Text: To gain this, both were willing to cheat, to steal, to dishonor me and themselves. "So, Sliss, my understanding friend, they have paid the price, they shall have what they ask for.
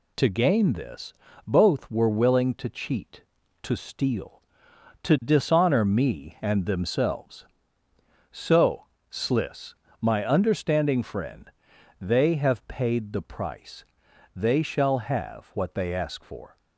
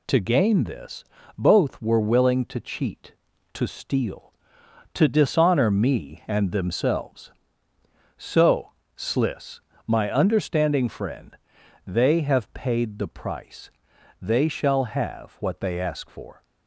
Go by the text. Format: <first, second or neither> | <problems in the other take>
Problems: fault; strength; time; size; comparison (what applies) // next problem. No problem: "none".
neither | none